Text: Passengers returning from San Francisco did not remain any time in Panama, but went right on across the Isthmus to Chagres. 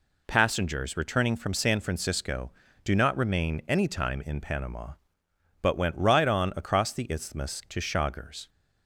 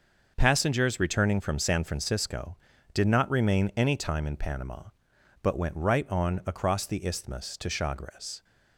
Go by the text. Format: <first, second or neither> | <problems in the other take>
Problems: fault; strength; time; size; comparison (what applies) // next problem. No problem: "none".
second | says "do" for "did"; at 2.8 s